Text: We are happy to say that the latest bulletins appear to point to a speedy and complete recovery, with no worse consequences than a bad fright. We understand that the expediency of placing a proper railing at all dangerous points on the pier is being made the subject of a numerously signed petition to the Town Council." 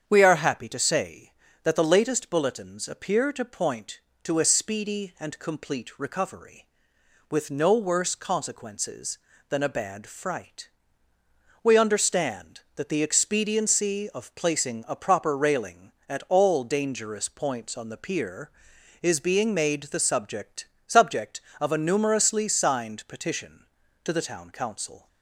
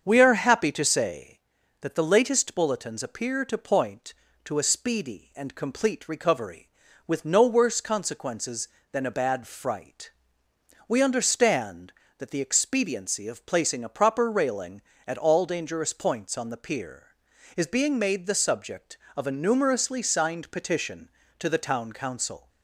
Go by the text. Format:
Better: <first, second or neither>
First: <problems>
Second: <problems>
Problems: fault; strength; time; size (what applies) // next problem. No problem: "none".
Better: second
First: starts louder than the rest; strong; until 1.0 s; 7.5 dB // says "subject" twice; at 20.8 s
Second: starts louder than the rest; until 1.1 s; 7 dB